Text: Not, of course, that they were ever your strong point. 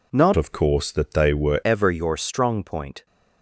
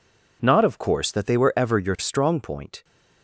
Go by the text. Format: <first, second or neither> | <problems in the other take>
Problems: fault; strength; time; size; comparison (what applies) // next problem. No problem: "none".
second | changes voice from "of" to "were"; from 0.3 to 1.6 s; 1.3 s long